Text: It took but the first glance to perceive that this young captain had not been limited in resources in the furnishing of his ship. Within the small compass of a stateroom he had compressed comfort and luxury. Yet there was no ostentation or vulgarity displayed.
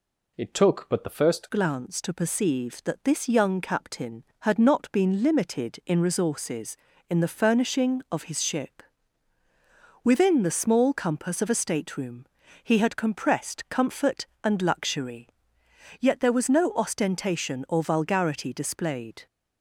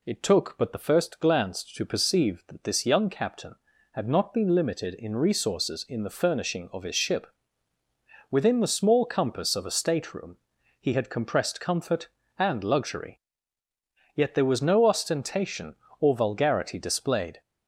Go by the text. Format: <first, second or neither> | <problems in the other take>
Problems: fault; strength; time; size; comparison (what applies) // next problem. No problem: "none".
second | changes voice at "glance"; from 1.4 s on; 17.8 s long // pauses between "stateroom" and "he"; at 12.2 s; 0.38 s long; also in the second